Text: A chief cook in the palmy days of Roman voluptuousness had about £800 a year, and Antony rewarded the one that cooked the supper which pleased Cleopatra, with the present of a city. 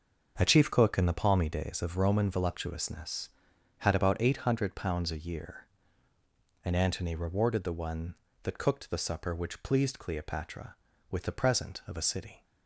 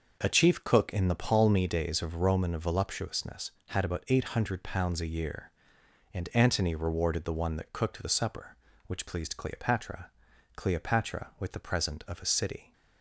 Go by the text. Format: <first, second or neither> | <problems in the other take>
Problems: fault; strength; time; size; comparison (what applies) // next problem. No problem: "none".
first | starts louder than the rest; noticeable; until 1.2 s; 6 dB; also in the first // says "Cleopatra" twice; at 10.5 s